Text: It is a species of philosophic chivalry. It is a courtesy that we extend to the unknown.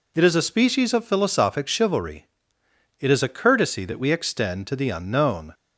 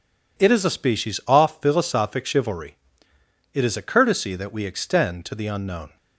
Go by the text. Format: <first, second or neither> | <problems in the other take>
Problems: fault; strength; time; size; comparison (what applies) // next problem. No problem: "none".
first | says "off" for "of"; at 1.2 s